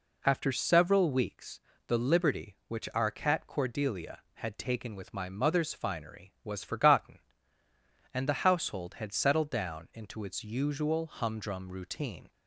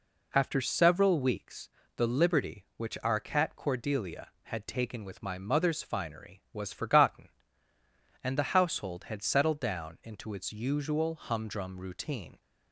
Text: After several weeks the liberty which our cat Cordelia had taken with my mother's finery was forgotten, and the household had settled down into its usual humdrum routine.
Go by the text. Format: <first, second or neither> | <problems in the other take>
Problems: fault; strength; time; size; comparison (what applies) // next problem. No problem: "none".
neither | pauses between "weeks" and "the"; slight; the same in both